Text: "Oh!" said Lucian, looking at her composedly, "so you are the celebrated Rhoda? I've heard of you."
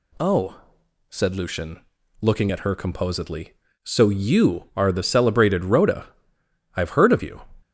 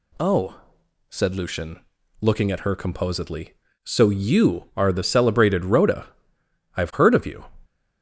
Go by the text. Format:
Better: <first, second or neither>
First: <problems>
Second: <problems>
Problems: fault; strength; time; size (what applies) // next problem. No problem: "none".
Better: neither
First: none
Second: none